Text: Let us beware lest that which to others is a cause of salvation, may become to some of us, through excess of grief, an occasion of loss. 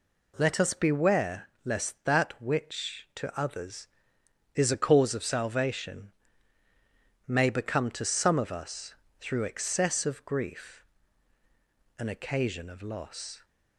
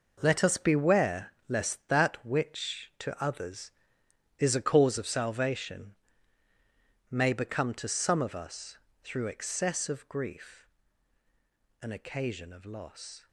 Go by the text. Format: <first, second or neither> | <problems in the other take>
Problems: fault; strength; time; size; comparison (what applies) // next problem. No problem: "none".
first | gets quieter; strong; throughout; 12 dB // pauses between "beware" and "lest"; slight; at 1.3 s; 0.16 s long; slight in the first